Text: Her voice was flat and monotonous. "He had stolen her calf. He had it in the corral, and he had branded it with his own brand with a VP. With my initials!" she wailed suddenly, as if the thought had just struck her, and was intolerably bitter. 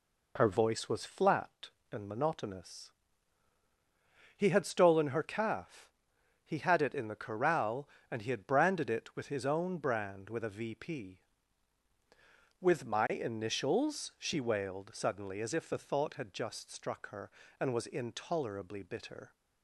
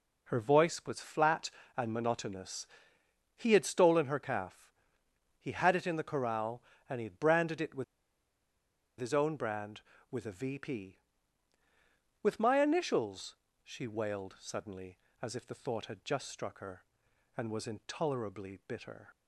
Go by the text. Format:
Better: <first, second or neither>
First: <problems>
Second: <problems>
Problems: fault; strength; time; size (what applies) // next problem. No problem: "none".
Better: first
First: none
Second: pauses between "with" and "his"; at 7.8 s; 1.1 s long